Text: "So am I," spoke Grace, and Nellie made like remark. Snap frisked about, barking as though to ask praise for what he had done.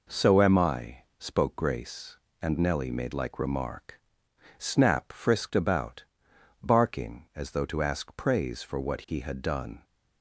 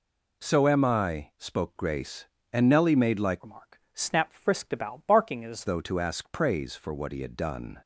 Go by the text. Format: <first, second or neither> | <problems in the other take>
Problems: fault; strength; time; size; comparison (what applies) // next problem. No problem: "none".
first | changes voice from "remark" to "as"; from 3.4 to 5.6 s; 2.2 s long